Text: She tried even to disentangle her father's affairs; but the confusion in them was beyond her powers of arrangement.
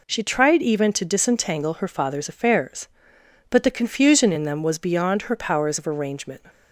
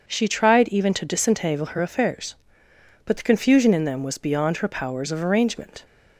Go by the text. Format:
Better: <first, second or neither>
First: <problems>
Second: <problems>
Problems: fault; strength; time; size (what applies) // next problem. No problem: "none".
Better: first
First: none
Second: starts louder than the rest; until 1.0 s; 6.5 dB // skips "father's"; at 1.7 s